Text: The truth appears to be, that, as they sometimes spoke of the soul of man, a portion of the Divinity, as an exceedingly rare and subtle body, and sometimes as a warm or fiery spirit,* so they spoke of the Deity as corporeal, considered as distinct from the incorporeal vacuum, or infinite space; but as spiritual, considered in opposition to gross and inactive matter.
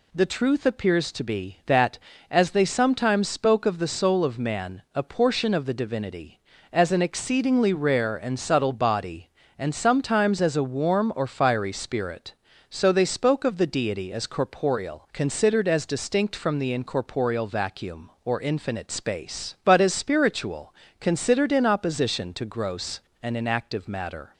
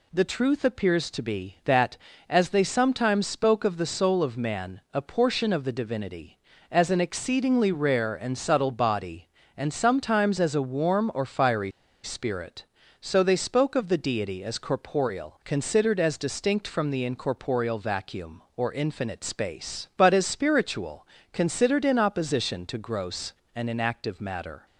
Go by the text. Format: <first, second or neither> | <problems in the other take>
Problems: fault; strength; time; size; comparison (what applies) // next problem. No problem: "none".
first | pauses between "fiery" and "spirit"; slight; at 11.6 s; 0.34 s long